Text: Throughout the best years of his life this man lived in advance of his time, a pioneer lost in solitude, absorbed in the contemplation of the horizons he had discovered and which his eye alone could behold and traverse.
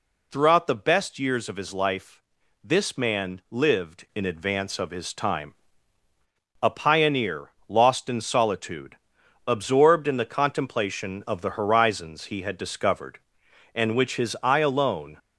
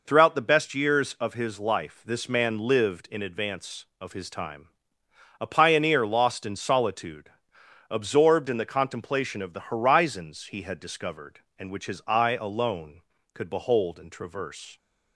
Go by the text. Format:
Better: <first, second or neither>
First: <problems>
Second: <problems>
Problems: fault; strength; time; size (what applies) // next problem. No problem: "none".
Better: second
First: pauses between "life" and "this"; at 2.1 s; 0.44 s long // pauses between "pioneer" and "lost"; slight; at 7.5 s; 0.18 s long // stops before "could behold and traverse"; at 15.1 s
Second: none